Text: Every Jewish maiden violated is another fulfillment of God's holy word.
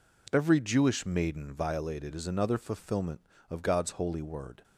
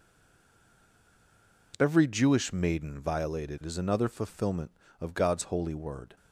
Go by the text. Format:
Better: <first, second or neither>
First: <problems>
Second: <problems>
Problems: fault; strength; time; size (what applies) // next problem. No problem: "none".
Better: first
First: none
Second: stays silent before the first word; noticeable; until 1.7 s; 1.7 s long